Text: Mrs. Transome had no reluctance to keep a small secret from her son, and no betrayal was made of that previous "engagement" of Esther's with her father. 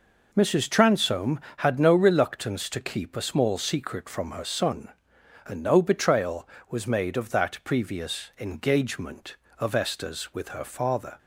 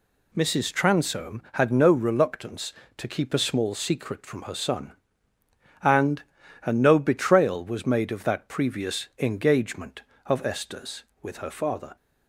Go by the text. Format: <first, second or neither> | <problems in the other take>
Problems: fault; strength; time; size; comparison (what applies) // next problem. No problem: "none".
first | says "and" twice; at 6.6 s